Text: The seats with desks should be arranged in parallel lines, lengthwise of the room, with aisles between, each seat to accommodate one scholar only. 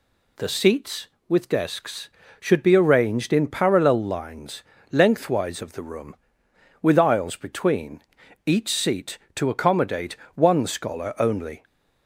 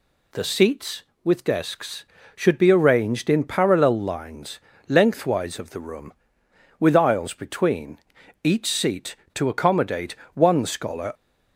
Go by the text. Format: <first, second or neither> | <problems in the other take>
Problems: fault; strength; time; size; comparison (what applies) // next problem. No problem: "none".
first | pauses between "accommodate" and "one"; slight; at 10.1 s; 0.18 s long; slight in the first // stops before "only"; at 11.1 s